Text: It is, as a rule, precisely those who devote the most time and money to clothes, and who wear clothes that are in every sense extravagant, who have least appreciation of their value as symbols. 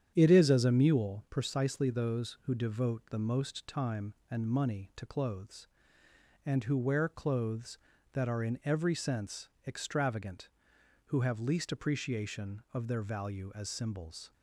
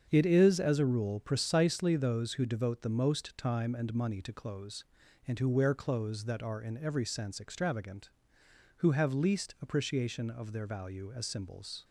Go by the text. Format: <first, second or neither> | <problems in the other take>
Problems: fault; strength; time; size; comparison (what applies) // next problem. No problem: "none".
second | starts louder than the rest; strong; until 1.1 s; 9 dB; strong in the second // says "mule" for "rule"; at 0.7 s // pauses between "sense" and "extravagant"; slight; at 9.4 s; 0.18 s long